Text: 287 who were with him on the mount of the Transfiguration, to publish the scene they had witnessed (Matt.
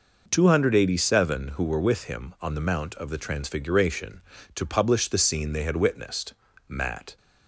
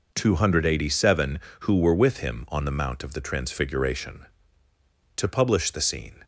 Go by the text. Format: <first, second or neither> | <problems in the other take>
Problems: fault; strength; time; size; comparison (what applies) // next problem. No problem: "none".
first | stops before "they had witnessed Matt"; at 6.2 s